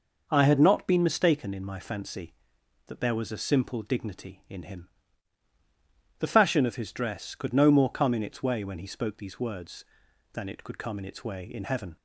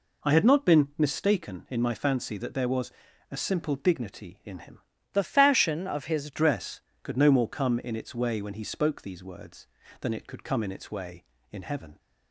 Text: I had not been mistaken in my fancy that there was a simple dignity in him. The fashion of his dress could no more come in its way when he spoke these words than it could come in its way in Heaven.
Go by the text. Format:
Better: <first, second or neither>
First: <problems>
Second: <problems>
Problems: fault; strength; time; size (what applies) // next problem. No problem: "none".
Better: first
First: none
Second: pauses between "was" and "a"; at 2.9 s; 0.40 s long // changes voice from "The" to "his"; from 5.1 to 6.3 s; 1.2 s long